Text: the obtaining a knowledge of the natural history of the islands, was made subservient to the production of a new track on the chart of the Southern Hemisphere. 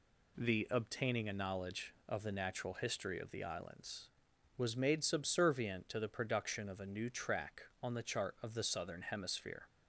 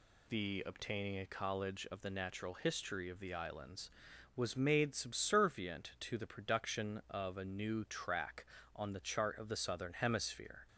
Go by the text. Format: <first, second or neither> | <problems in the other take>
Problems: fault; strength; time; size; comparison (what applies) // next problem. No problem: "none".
first | says "college" for "knowledge"; at 1.2 s